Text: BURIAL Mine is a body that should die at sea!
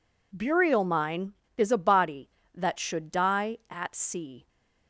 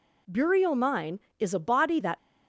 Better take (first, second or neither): first